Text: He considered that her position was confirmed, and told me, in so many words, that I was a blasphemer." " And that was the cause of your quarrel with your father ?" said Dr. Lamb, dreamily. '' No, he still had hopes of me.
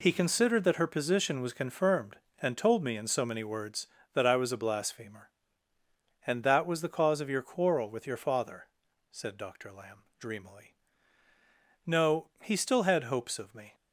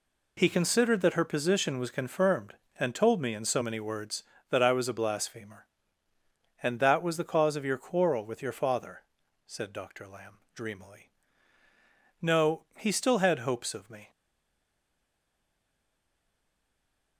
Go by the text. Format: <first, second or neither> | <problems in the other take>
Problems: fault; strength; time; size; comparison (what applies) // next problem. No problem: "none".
first | stays silent after the last word; strong; from 14.0 s on; 3.1 s long